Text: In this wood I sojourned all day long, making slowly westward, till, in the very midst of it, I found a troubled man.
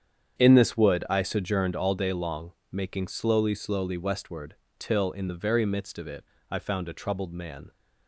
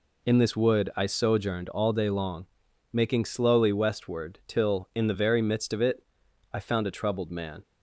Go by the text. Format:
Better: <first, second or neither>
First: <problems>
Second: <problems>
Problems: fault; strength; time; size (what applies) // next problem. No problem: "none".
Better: second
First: starts louder than the rest; strong; until 1.4 s; 8 dB // says "slowly" twice; at 3.5 s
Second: none